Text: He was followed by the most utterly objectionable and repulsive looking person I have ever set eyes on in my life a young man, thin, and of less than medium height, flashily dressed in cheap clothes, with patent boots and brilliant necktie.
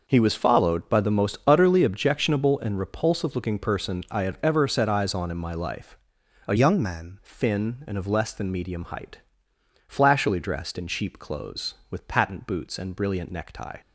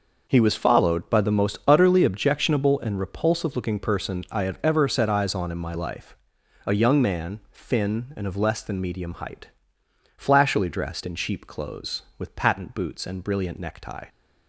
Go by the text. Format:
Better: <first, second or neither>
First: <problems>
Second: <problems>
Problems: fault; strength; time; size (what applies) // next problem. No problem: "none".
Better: second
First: pauses between "life" and "a"; noticeable; at 5.9 s; 0.52 s long // changes voice from "young" to "man"; from 6.5 to 7.1 s; 0.6 s long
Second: pauses between "life" and "a"; noticeable; at 6.1 s; 0.52 s long